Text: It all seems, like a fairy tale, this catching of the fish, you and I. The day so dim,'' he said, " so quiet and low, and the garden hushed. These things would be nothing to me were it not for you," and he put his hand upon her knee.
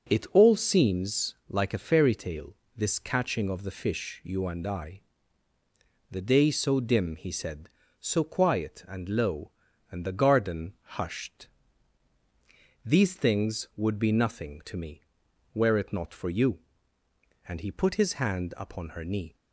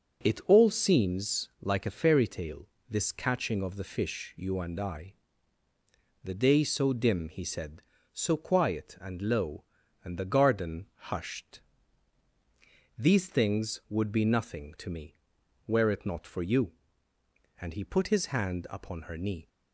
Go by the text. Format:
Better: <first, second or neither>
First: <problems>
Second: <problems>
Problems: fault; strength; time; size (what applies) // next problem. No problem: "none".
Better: neither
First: starts louder than the rest; until 1.1 s; 7 dB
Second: starts louder than the rest; until 1.3 s; 7 dB